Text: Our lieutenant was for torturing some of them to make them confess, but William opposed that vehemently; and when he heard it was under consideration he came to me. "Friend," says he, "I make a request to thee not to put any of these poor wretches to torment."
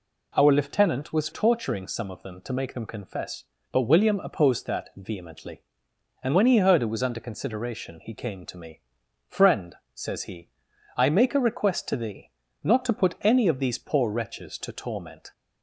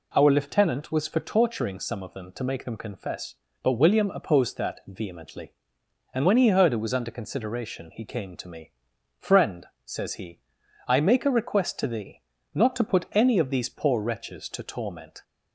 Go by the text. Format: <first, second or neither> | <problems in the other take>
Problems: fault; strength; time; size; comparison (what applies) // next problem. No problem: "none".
second | skips "for"; at 1.3 s // pauses between "thee" and "not"; slight; at 12.3 s; 0.30 s long; slight in the second